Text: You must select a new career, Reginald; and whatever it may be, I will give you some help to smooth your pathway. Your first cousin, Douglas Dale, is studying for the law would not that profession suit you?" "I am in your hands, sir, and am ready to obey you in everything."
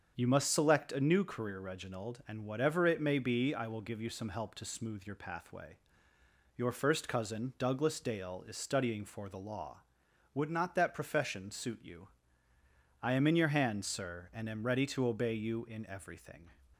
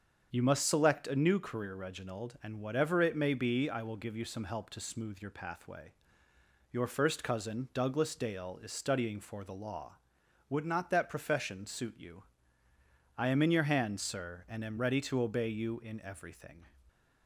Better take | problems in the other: neither | starts louder than the rest; the same in both

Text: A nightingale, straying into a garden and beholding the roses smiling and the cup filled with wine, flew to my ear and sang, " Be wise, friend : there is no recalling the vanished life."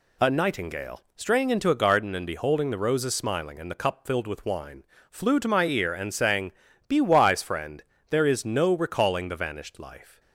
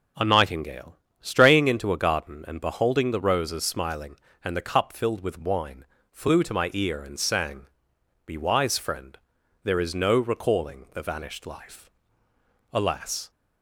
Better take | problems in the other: first | goes on to say "Alas"; from 12.7 s on; 0.58 s long

